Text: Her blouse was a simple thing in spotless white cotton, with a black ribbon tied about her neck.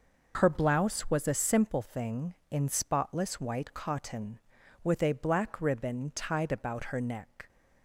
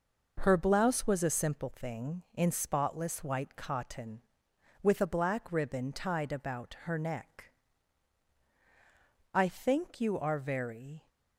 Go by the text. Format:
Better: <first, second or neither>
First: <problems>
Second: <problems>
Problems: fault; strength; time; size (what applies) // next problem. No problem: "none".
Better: first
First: none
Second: goes on to say "I think you are very"; strong; from 9.3 s on; 1.7 s long